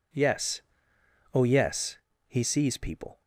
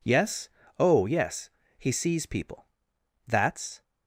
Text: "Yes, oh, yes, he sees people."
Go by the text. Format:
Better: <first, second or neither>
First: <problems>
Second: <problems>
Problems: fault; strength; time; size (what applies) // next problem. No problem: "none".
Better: first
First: none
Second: goes on to say "That's"; from 3.2 s on; 0.58 s long